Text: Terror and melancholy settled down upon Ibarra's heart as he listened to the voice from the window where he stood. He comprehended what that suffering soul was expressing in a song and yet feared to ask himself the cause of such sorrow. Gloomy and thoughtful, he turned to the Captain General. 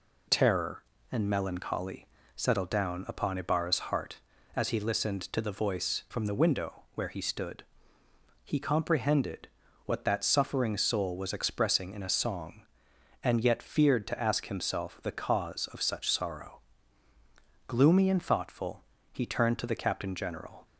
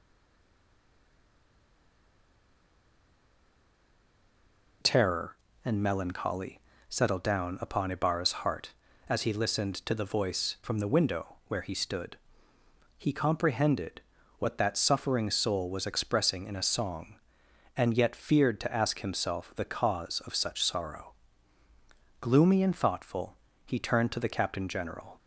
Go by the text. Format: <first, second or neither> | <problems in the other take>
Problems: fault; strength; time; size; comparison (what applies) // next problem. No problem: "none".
first | stays silent before the first word; strong; until 4.8 s; 4.8 s long // pauses between "melancholy" and "settled"; slight; at 6.5 s; 0.30 s long; slight in the first // pauses between "comprehended" and "what"; at 13.9 s; 0.38 s long; also in the first